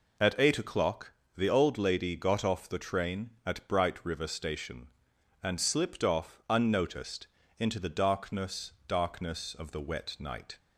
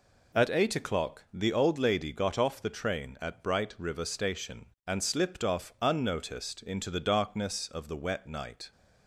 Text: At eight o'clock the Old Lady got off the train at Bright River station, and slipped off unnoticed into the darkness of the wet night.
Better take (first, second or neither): second